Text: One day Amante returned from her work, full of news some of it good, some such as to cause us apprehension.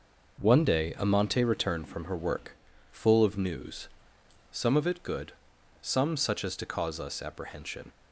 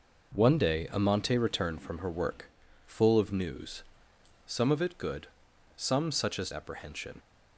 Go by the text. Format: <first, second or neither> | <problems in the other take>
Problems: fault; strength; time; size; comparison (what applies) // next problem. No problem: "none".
first | pauses between "news" and "some"; noticeable; at 3.8 s; 0.64 s long; noticeable in the first // skips "to cause us"; at 6.5 s